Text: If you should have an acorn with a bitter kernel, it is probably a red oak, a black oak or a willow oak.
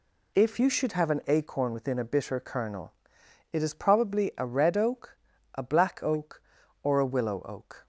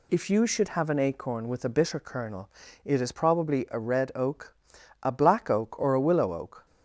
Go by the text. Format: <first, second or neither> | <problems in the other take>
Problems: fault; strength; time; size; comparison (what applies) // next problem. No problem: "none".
second | says "within" for "with"; at 1.7 s